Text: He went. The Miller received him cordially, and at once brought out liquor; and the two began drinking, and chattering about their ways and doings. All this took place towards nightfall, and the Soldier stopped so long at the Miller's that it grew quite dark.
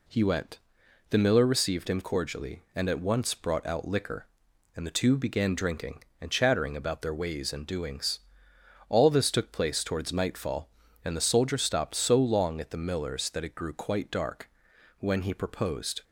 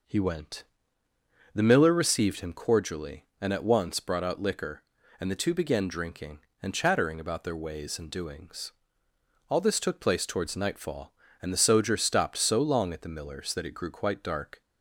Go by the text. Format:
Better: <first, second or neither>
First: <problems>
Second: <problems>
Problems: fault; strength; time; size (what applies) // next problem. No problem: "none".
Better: second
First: goes on to say "When he proposed"; noticeable; from 14.9 s on; 1.0 s long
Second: none